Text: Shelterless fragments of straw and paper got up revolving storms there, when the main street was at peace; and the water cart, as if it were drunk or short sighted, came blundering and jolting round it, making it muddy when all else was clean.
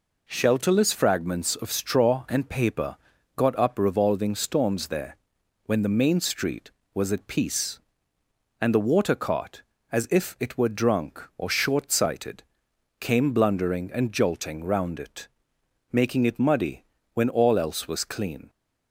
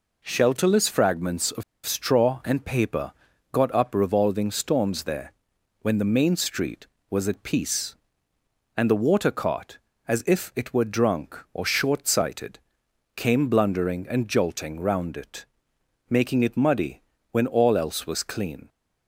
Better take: first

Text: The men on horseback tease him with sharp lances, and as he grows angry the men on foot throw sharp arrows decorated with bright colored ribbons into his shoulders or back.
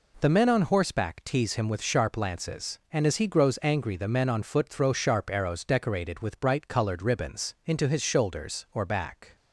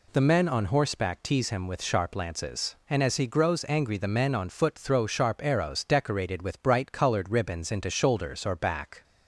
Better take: first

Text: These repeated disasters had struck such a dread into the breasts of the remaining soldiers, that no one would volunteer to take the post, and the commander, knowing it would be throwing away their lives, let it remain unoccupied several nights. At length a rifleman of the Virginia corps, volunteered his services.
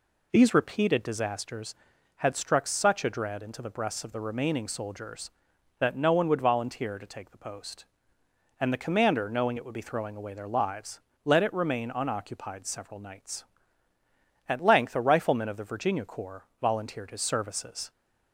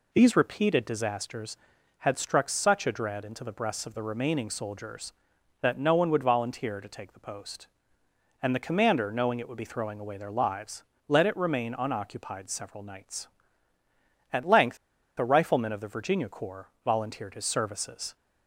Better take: first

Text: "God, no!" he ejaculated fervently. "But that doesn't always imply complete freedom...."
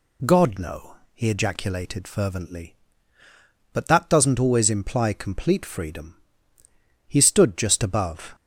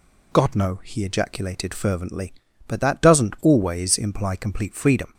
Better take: second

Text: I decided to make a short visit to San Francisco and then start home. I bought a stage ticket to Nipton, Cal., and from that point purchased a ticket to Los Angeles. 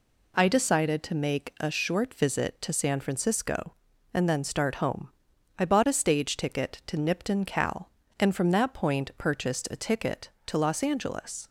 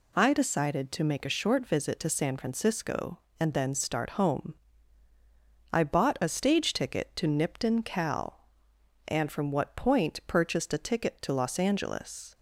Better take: first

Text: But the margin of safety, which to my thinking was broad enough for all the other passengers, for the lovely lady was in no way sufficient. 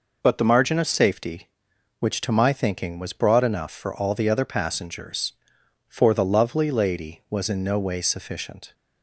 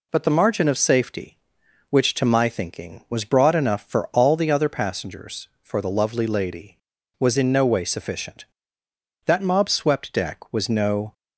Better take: first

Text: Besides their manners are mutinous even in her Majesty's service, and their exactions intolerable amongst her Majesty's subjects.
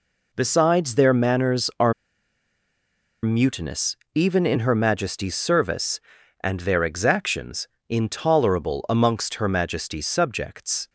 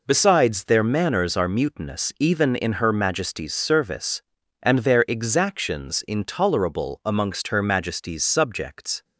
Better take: second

